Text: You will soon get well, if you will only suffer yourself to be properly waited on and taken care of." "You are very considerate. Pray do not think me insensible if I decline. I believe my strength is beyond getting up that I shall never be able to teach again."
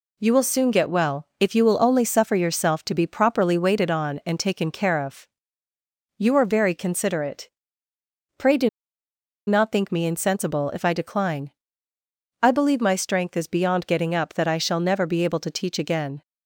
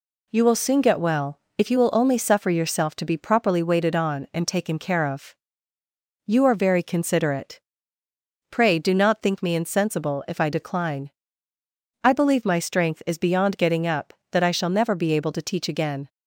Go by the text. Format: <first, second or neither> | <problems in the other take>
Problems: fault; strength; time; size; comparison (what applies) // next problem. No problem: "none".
second | pauses between "do" and "not"; noticeable; at 8.6 s; 0.79 s long